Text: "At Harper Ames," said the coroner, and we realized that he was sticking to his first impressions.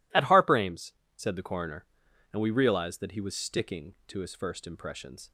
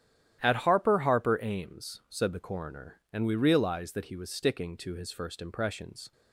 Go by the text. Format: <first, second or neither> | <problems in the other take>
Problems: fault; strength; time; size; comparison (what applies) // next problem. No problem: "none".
first | starts louder than the rest; strong; until 1.4 s; 11 dB // says "Harper" twice; at 0.9 s